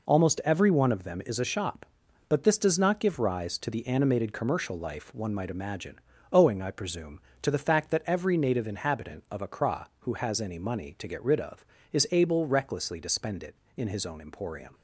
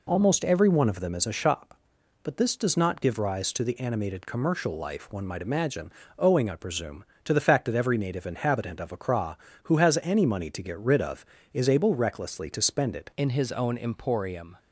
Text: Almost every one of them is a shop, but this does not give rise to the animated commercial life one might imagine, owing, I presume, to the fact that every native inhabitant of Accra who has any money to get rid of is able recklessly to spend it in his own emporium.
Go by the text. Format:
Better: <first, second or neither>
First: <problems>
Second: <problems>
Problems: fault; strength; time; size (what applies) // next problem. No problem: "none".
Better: first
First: none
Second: changes voice at "in"; from 13.1 s on; 1.4 s long